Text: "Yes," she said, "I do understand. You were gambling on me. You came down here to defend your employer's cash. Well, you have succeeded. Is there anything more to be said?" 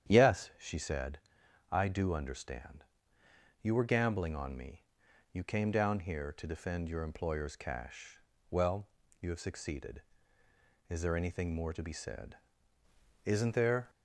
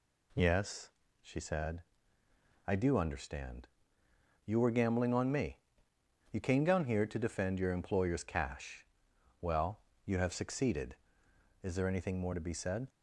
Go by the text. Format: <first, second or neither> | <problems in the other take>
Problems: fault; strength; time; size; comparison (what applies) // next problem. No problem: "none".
second | starts louder than the rest; strong; until 1.1 s; 9.5 dB // goes on to say "Isn't there"; noticeable; from 13.2 s on; 0.64 s long